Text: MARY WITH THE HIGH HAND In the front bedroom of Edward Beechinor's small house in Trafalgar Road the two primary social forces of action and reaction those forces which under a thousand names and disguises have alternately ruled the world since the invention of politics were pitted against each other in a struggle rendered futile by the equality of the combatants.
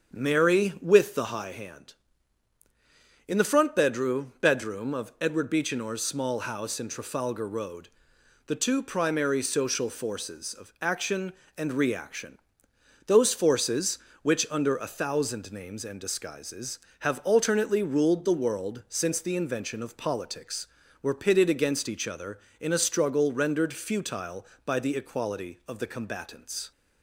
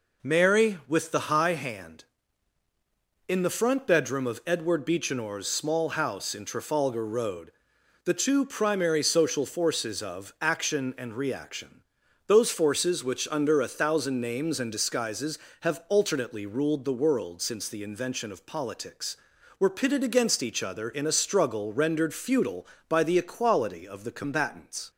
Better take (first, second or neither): second